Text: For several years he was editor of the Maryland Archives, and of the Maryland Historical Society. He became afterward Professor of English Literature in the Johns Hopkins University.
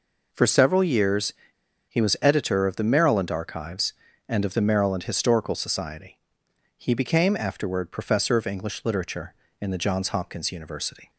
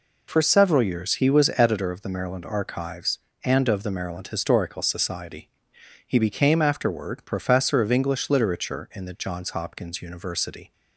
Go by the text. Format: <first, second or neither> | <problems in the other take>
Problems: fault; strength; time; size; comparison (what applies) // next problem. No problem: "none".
second | pauses between "years" and "he"; noticeable; at 1.3 s; 0.54 s long